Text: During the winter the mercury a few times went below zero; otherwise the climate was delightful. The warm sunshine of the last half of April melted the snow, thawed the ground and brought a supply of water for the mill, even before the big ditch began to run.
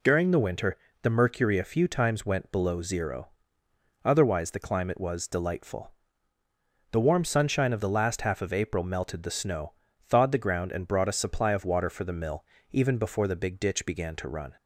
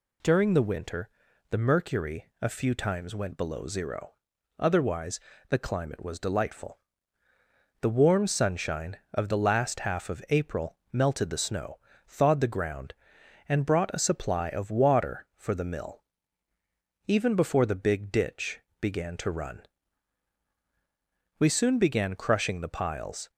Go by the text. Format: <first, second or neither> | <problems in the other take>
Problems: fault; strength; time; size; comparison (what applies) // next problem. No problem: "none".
first | pauses between "winter" and "the"; at 1.0 s; 0.42 s long; slight in the first // pauses between "otherwise" and "the"; slight; at 5.2 s; 0.30 s long // pauses between "April" and "melted"; slight; at 10.7 s; 0.16 s long // pauses between "ditch" and "began"; slight; at 18.5 s; 0.22 s long // goes on to say "We soon began crushing the piles"; strong; from 21.3 s on; 1.9 s long